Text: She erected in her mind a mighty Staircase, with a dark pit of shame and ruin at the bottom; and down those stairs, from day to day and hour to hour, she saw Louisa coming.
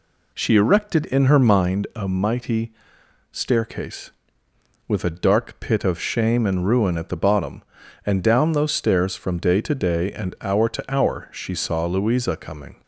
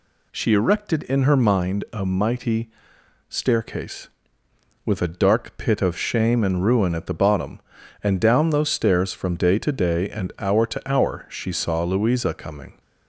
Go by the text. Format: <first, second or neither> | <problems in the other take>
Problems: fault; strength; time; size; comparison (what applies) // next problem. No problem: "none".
second | starts louder than the rest; slight; until 1.9 s; 2.5 dB // pauses between "mighty" and "Staircase"; noticeable; at 2.7 s; 0.62 s long; noticeable in the second